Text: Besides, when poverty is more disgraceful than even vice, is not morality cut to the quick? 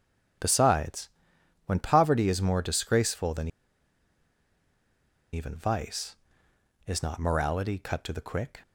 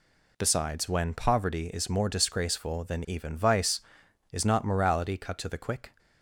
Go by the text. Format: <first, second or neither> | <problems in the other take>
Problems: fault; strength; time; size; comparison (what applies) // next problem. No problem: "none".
second | starts louder than the rest; strong; until 1.9 s; 9 dB // pauses between "than" and "even"; strong; at 3.4 s; 1.8 s long